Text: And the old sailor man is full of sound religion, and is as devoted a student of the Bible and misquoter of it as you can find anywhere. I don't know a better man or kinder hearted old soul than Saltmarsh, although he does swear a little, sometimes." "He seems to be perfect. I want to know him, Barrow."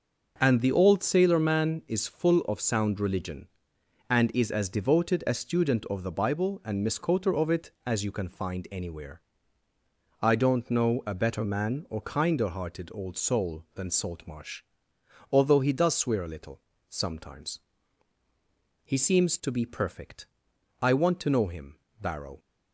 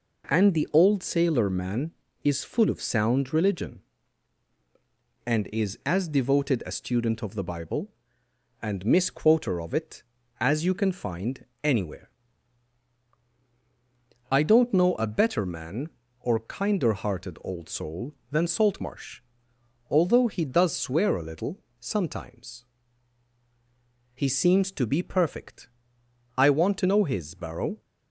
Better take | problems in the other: first | pauses between "find" and "anywhere"; slight; at 11.4 s; 0.18 s long // says "his" for "him"; at 27.0 s

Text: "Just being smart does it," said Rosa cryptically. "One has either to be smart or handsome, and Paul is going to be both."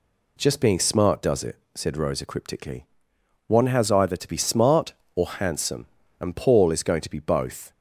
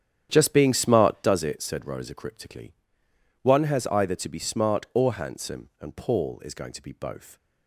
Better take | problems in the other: first | starts louder than the rest; strong; until 1.3 s; 9.5 dB

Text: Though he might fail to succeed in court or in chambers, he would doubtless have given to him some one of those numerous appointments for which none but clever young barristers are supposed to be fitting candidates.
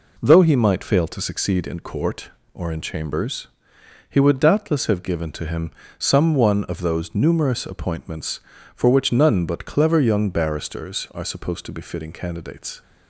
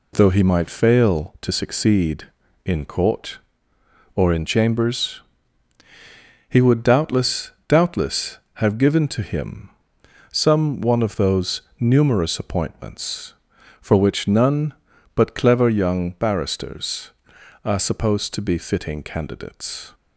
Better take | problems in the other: first | says "doubtless" twice; at 7.6 s // pauses between "him" and "some"; noticeable; at 9.7 s; 0.60 s long; slight in the first // pauses between "those" and "numerous"; slight; at 11.6 s; 0.18 s long

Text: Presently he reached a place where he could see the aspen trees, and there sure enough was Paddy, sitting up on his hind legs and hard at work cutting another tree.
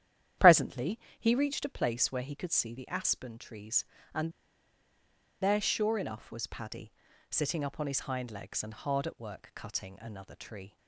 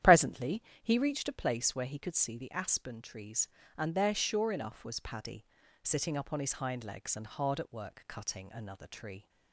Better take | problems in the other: second | starts louder than the rest; strong; until 1.6 s; 10.5 dB; strong in the second // pauses between "Presently" and "he"; slight; at 0.9 s; 0.22 s long; slight in the second // pauses between "and" and "there"; at 4.3 s; 1.1 s long

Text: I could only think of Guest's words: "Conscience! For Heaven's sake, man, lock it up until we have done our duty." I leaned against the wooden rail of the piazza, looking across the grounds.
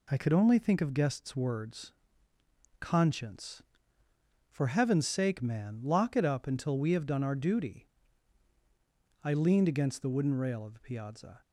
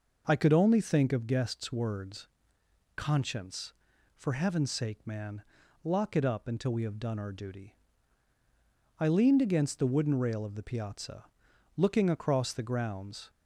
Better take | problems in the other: second | stops before "looking across the grounds"; at 11.4 s

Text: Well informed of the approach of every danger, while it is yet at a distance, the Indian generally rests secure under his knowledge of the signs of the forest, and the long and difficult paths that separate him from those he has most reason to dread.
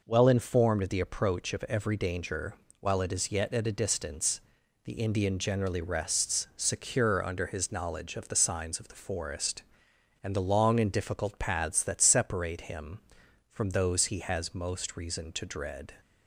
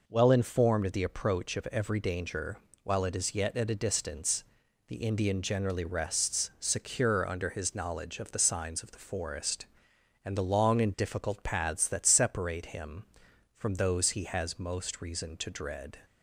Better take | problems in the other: neither | none

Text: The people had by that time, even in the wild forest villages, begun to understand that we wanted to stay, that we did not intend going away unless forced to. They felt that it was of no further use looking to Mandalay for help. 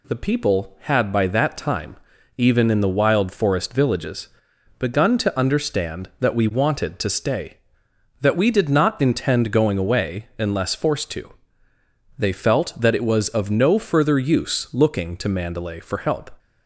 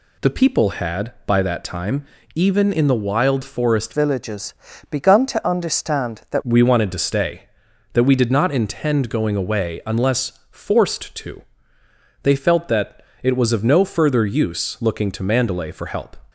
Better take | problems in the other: first | changes voice from "villages" to "that"; from 3.9 to 6.4 s; 2.5 s long // pauses between "that" and "it"; slight; at 13.0 s; 0.20 s long

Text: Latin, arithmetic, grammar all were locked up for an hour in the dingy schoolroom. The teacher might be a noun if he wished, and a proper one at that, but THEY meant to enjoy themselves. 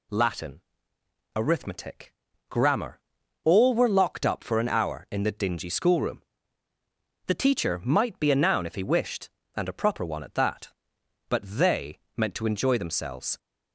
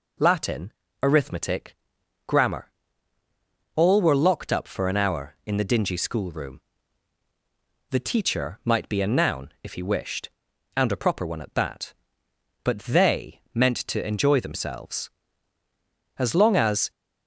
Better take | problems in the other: first | pauses between "grammar" and "all"; at 2.7 s; 1.0 s long; also in the first // pauses between "THEY" and "meant"; slight; at 13.3 s; 0.16 s long; slight in the first // goes on to say "As long as"; noticeable; from 16.1 s on; 0.72 s long

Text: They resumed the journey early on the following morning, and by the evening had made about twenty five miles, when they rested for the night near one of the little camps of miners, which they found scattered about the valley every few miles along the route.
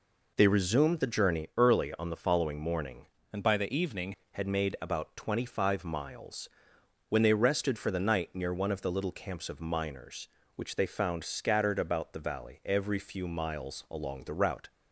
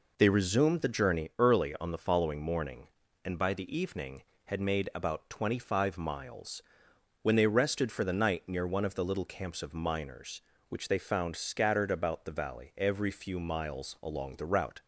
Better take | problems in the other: second | changes voice from "and" to "evening"; from 3.3 to 4.1 s; 0.8 s long

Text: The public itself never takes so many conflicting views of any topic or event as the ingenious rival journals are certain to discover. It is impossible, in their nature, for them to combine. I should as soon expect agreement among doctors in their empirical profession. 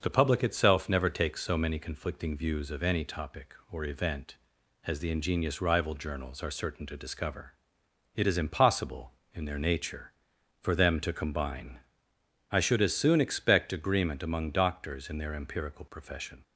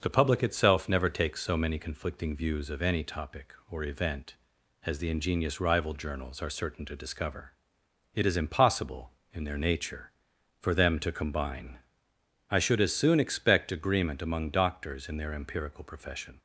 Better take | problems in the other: neither | starts louder than the rest; the same in both

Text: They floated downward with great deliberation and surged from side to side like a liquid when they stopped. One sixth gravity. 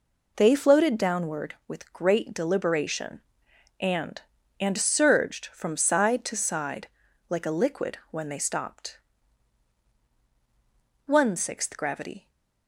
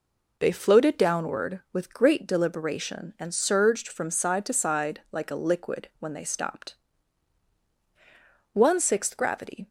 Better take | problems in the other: second | says "and" twice; at 4.5 s // pauses between "side" and "like"; at 6.8 s; 0.42 s long

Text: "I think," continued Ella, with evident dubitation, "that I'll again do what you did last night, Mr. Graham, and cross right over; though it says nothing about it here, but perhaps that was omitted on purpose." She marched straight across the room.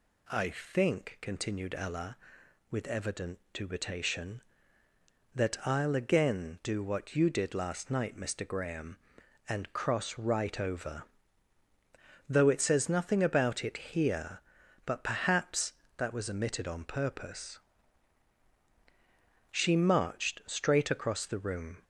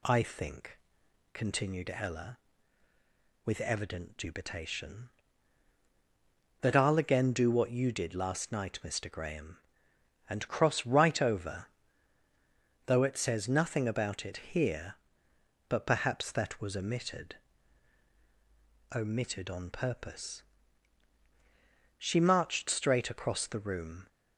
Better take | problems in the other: first | says "omitted" twice; at 18.9 s

